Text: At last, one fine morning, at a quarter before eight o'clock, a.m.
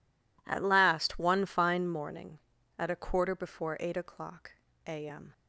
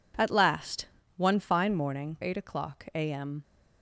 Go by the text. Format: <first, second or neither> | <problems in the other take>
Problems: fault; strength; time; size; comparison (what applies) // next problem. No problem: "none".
first | skips "at a quarter before"; at 2.1 s